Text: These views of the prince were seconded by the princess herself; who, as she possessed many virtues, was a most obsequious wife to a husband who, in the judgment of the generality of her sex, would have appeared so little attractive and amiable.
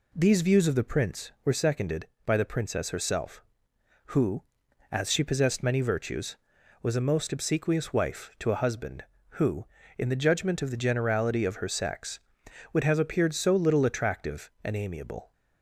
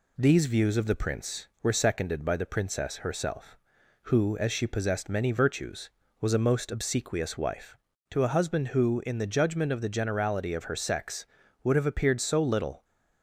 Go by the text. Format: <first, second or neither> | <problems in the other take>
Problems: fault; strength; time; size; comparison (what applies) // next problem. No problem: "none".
first | stops before "attractive and amiable"; at 12.8 s